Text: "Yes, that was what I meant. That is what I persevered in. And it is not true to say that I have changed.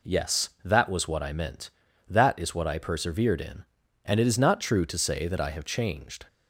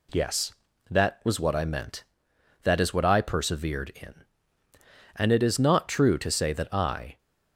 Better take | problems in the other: first | stops before "have changed"; at 7.1 s

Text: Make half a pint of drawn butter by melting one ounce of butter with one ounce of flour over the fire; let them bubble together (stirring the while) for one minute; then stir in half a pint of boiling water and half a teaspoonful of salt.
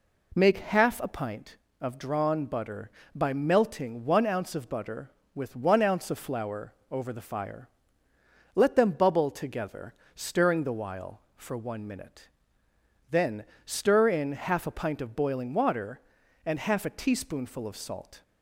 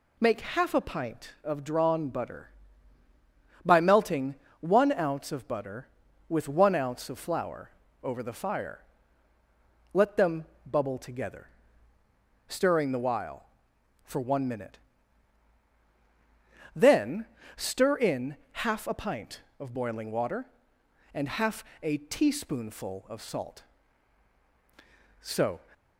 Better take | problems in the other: first | pauses between "melting" and "one"; slight; at 4.3 s; 0.26 s long // pauses between "flour" and "over"; slight; at 7.6 s; 0.32 s long; slight in the first // pauses between "them" and "bubble"; slight; at 10.4 s; 0.20 s long // pauses between "then" and "stir"; slight; at 17.2 s; 0.32 s long; slight in the first // pauses between "in" and "half"; slight; at 18.3 s; 0.26 s long // pauses between "half" and "a"; slight; at 21.6 s; 0.18 s long // goes on to say "So"; slight; from 25.1 s on; 0.38 s long

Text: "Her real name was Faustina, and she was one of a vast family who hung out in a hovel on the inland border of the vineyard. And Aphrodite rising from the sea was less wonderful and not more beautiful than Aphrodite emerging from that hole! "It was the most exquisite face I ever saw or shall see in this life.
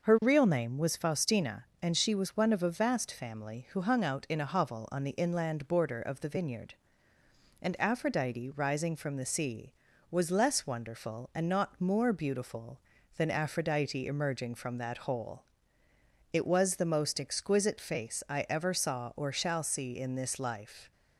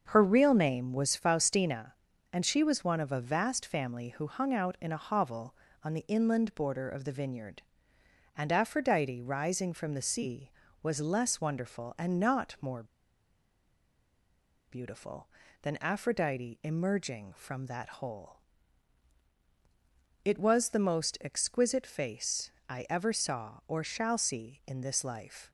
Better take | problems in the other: first | starts louder than the rest; until 1.1 s; 6.5 dB; noticeable in the first // pauses between "more" and "beautiful"; strong; at 12.8 s; 1.8 s long // pauses between "face" and "I"; slight; at 22.5 s; 0.16 s long

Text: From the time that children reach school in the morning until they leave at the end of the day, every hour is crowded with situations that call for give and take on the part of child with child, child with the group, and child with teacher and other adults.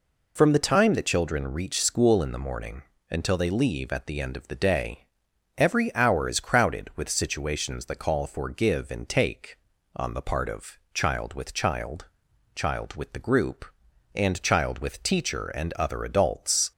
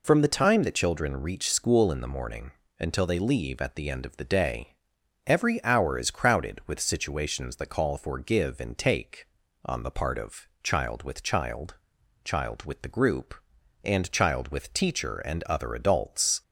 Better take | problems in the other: neither | pauses between "morning" and "until"; slight; the same in both // pauses between "of" and "child"; slight; the same in both

